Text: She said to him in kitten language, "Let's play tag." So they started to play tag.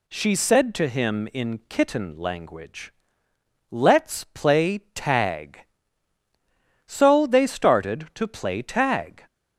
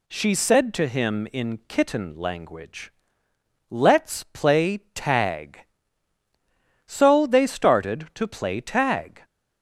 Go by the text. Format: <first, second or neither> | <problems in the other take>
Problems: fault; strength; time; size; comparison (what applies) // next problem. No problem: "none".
neither | pauses between "play" and "tag"; slight; the same in both